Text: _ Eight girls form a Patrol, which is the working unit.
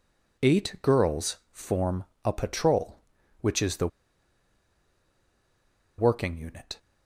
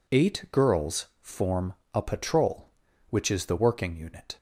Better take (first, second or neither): second